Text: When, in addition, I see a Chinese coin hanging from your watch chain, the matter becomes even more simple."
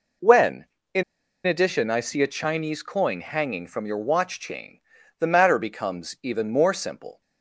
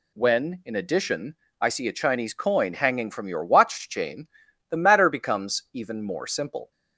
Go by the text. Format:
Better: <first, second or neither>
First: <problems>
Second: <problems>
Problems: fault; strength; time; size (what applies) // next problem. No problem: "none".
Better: second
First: pauses between "in" and "addition"; at 1.0 s; 0.43 s long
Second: none